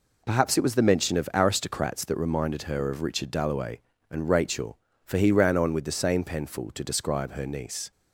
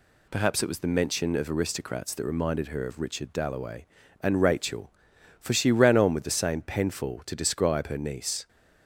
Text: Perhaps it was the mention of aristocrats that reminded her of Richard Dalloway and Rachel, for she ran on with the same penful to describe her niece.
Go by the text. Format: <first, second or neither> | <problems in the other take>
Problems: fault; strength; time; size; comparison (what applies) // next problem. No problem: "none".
second | says "he" for "she"; at 5.1 s